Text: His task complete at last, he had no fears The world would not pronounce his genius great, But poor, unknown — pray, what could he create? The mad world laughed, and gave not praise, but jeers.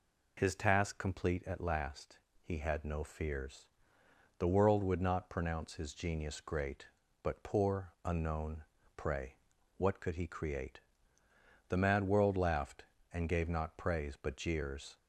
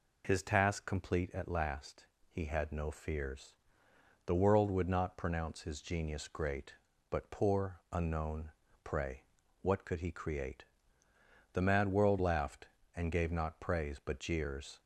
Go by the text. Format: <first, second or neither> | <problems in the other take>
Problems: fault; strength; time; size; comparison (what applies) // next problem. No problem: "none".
neither | pauses between "fears" and "The"; noticeable; the same in both